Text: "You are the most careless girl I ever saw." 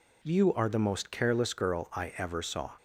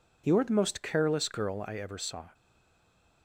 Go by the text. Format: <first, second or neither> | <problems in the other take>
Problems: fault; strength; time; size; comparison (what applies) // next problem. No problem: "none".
first | stays silent after the last word; slight; from 2.3 s on; 0.9 s long